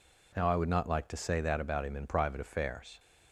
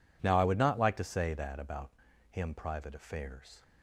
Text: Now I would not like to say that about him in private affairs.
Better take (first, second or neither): first